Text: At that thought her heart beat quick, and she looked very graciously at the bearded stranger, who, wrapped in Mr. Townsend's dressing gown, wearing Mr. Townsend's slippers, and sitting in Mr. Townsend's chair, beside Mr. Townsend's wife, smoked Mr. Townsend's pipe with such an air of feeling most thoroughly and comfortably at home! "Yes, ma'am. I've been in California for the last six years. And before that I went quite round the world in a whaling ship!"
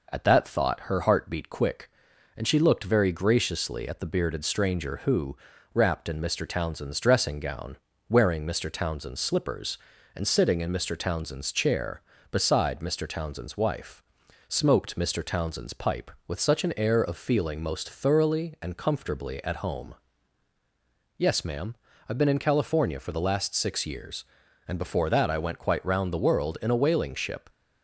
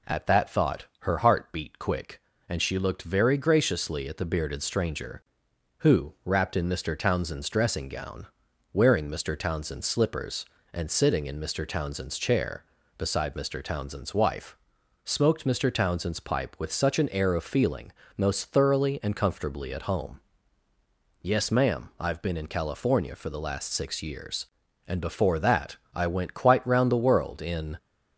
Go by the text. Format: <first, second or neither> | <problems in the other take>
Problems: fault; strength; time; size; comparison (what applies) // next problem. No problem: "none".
first | pauses between "feeling" and "most"; slight; at 17.9 s; 0.26 s long // pauses between "that" and "I"; slight; at 25.7 s; 0.18 s long // stops before "a whaling ship"; at 27.7 s